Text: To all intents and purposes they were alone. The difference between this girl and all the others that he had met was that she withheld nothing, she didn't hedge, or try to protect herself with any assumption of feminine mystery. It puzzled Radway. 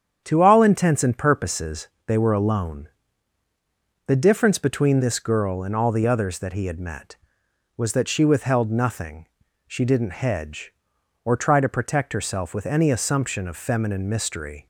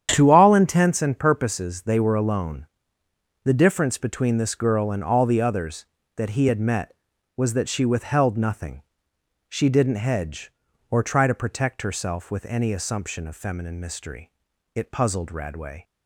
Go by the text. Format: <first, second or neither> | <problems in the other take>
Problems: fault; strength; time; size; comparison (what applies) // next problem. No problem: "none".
second | starts louder than the rest; strong; until 1.2 s; 8.5 dB; strong in the second // pauses between "purposes" and "they"; slight; at 1.8 s; 0.20 s long // stops before "It puzzled Radway"; at 14.6 s